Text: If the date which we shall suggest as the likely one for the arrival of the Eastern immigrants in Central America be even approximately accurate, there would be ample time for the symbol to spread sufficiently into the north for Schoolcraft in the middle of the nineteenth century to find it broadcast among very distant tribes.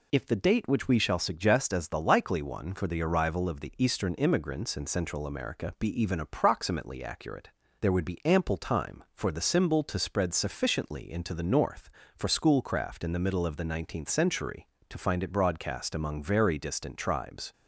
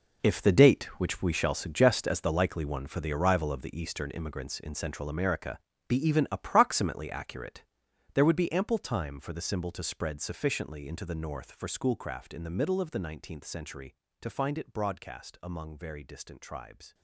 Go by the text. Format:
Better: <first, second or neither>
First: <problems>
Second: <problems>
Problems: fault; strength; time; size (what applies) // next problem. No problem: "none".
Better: first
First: none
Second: gets quieter; strong; throughout; 13 dB // pauses between "America" and "be"; slight; at 5.5 s; 0.30 s long